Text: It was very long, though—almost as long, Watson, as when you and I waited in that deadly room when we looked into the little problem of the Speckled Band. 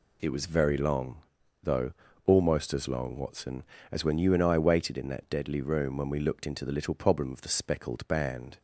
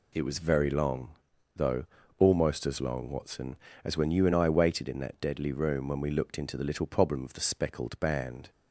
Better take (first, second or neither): neither